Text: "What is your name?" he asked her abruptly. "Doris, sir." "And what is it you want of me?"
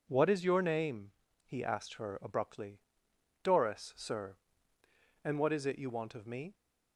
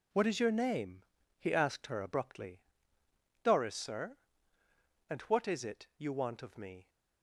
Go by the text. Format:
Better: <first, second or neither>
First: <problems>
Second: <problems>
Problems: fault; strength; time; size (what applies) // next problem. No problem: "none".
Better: neither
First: none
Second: none